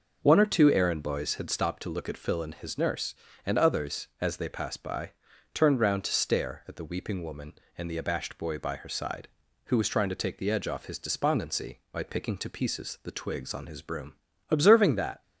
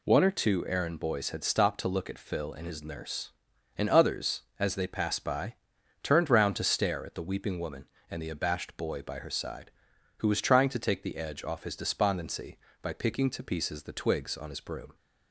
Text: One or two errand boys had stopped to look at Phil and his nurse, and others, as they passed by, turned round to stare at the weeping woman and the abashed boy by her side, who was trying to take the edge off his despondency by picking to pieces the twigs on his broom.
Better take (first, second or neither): second